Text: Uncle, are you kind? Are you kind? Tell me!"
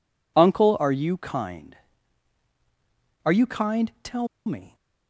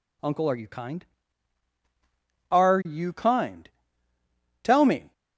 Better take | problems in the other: second | pauses between "Tell" and "me"; slight; at 4.2 s; 0.19 s long

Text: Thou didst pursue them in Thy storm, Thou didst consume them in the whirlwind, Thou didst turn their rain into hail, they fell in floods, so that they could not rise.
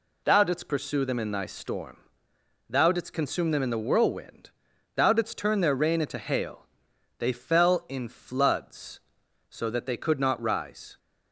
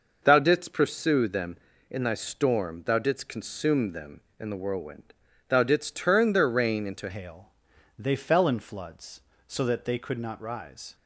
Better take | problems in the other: first | changes voice at "hail"; from 7.0 s on; 3.9 s long

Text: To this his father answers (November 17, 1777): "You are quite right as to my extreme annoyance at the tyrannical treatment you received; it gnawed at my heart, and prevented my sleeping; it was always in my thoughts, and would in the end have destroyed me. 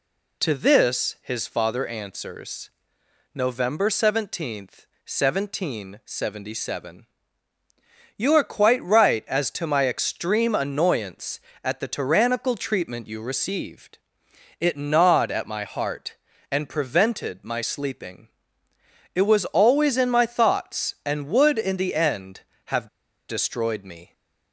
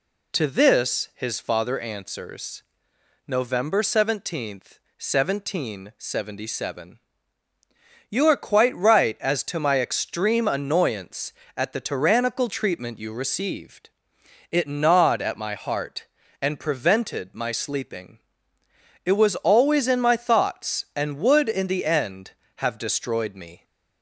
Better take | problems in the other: second | pauses between "have" and "destroyed"; at 22.8 s; 0.42 s long

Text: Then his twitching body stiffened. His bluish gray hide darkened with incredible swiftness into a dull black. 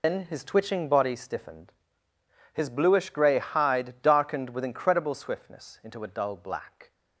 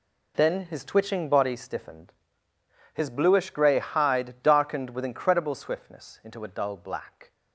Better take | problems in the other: second | loses the start of "Then"; at 0.0 s; 90 ms

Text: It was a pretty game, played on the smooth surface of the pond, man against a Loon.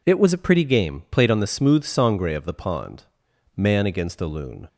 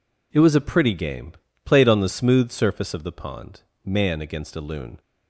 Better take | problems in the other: second | says "sangre" for "surface"; at 1.8 s

